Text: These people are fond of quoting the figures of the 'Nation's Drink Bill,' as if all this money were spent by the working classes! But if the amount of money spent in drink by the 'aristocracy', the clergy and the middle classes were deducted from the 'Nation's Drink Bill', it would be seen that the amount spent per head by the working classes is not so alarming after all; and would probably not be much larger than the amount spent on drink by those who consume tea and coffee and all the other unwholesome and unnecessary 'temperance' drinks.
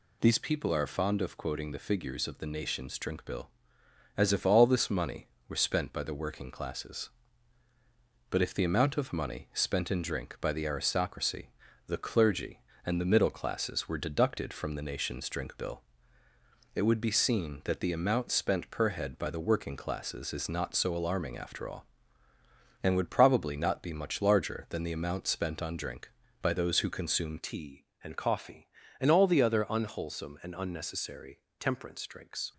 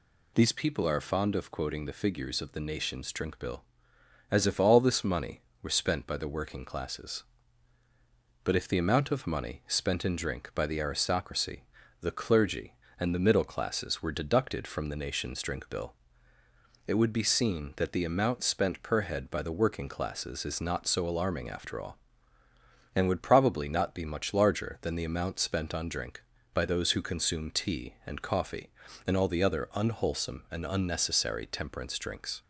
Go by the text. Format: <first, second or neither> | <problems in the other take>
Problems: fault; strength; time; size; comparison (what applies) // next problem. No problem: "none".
second | changes voice at "tea"; from 27.3 s on; 5.2 s long // pauses between "unnecessary" and "temperance"; slight; at 31.4 s; 0.18 s long